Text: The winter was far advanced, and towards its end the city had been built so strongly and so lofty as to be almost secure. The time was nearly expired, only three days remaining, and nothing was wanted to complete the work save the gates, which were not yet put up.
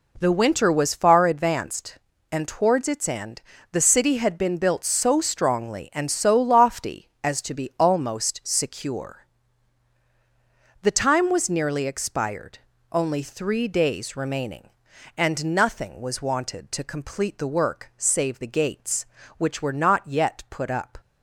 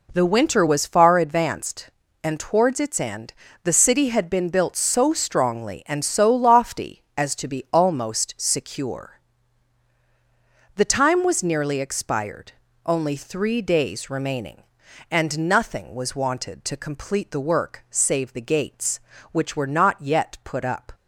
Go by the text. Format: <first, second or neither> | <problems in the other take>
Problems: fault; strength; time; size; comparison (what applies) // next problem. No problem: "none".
neither | pauses between "end" and "the"; slight; the same in both